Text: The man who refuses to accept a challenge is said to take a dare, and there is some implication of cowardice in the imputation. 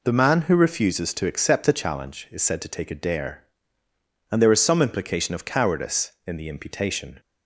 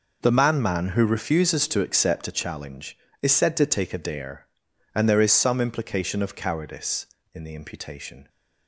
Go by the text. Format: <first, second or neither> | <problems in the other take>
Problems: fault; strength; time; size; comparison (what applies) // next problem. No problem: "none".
first | says "man" twice; at 0.6 s